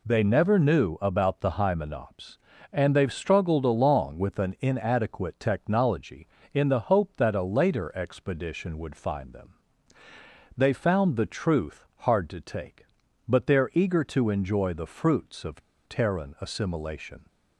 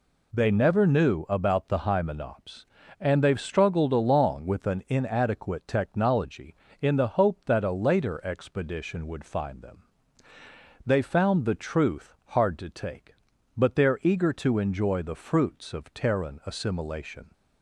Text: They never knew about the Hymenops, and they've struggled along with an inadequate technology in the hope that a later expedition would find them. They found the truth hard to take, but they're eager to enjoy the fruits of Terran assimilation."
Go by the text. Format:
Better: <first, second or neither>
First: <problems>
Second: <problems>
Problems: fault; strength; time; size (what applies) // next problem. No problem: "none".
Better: second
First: pauses between "of" and "Terran"; slight; at 15.6 s; 0.25 s long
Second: none